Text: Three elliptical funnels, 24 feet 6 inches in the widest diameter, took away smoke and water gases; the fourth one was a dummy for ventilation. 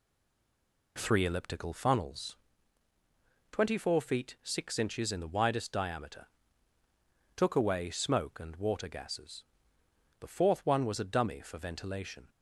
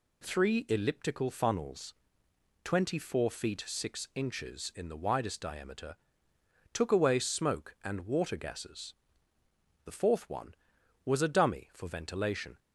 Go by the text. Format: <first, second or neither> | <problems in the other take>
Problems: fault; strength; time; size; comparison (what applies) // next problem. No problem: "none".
second | stays silent before the first word; slight; until 0.9 s; 0.9 s long